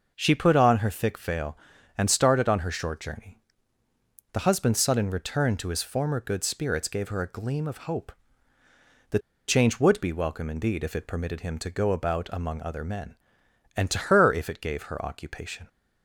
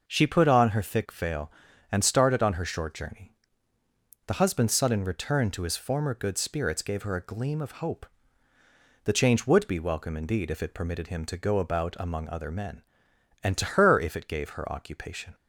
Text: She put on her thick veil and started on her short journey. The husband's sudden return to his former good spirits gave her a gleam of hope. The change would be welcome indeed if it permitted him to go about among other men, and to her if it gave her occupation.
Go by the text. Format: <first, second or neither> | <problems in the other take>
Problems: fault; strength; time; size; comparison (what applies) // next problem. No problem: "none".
second | starts louder than the rest; noticeable; until 1.1 s; 6 dB; noticeable in the second // pauses between "The" and "change"; slight; at 9.1 s; 0.28 s long